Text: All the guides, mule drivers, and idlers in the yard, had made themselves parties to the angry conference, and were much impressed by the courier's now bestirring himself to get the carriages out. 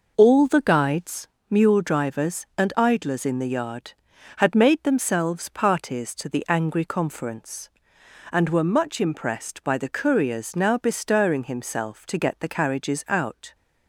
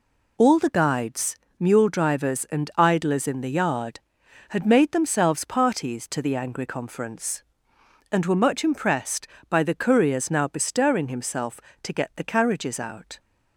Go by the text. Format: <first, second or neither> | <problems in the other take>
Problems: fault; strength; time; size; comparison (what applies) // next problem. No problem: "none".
neither | none